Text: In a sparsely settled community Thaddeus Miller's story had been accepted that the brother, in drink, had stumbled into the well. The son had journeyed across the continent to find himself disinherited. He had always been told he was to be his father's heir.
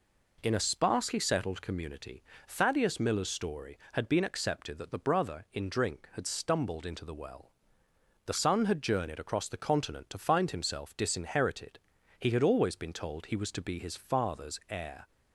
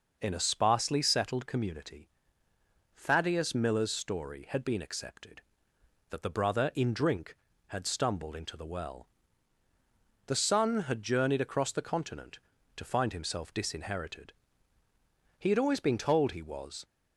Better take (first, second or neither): first